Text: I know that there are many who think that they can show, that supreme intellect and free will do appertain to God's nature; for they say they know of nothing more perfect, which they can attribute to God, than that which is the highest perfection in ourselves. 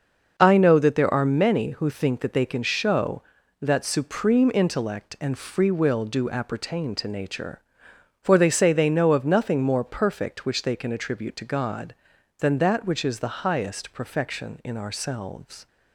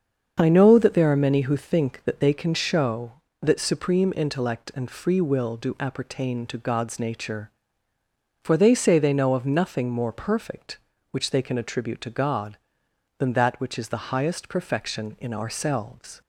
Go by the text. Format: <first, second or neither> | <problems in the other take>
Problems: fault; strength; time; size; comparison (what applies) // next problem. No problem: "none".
second | starts louder than the rest; noticeable; until 1.3 s; 6 dB; also in the second // skips "God's"; at 7.0 s